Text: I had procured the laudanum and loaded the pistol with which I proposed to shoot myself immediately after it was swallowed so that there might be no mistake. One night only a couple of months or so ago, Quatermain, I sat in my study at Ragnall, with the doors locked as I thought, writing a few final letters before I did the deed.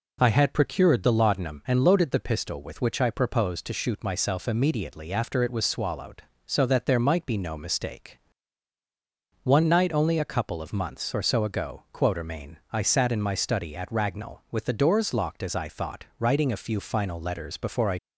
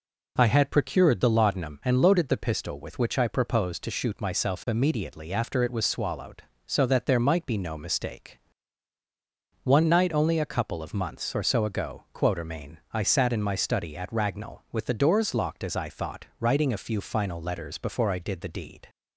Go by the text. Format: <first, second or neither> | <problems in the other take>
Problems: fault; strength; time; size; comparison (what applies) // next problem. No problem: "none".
second | stops before "did the deed"; at 17.9 s